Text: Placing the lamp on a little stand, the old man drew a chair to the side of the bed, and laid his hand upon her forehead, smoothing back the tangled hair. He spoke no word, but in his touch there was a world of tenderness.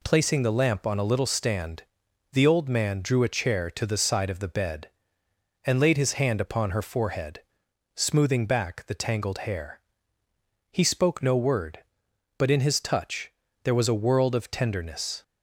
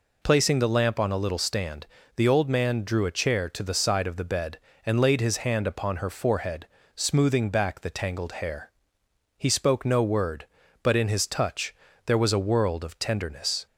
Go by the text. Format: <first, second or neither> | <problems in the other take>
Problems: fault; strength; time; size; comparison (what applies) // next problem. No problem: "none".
neither | pauses between "touch" and "there"; slight; the same in both